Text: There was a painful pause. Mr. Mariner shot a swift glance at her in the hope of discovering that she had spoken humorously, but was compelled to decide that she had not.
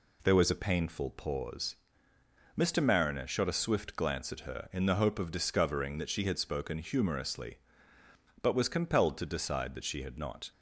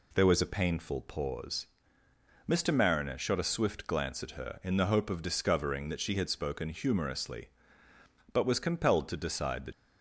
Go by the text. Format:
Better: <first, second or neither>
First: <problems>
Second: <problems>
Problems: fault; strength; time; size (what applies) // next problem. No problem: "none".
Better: first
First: none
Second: stops before "she had not"; at 9.7 s